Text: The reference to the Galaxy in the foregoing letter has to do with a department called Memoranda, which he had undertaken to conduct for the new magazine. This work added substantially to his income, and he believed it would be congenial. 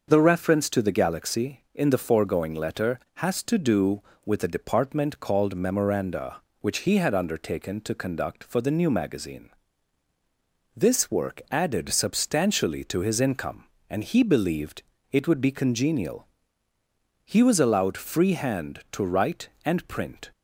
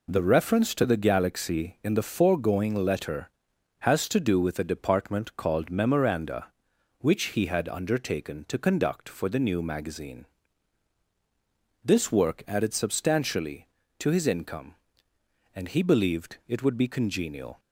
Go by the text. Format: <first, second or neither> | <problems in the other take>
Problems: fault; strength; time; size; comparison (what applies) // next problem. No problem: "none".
second | starts louder than the rest; until 1.0 s; 6.5 dB // pauses between "believed" and "it"; slight; at 14.8 s; 0.30 s long // goes on to say "He was allowed free hand to write and print"; strong; from 17.2 s on; 3.0 s long